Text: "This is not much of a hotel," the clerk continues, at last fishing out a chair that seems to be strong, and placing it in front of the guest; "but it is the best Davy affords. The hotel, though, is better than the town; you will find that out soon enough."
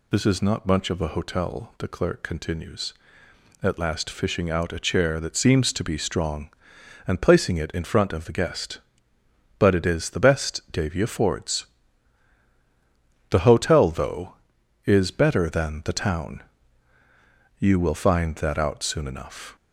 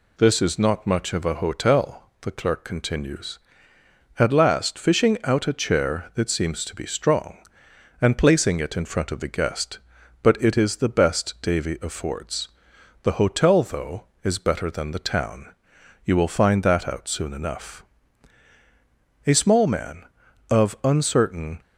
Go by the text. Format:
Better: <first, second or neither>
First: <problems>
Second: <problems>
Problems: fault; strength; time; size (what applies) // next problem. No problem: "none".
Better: first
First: none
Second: goes on to say "A small man of uncertain"; strong; from 19.2 s on; 2.3 s long